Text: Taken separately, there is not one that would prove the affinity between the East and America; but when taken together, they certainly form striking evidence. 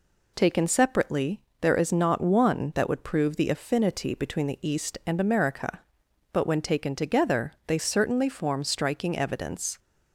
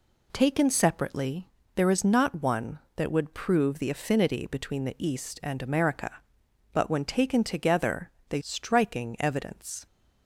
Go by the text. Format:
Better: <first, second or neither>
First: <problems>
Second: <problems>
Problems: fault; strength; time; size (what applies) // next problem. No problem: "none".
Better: first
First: none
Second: skips "certainly form"; at 8.3 s